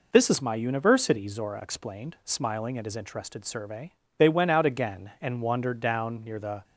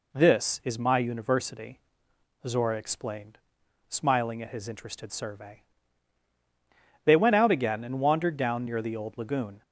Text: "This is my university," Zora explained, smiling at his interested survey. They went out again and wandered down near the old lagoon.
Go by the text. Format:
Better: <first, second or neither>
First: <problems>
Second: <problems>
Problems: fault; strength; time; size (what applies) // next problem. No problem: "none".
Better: second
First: stops before "old lagoon"; at 6.6 s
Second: none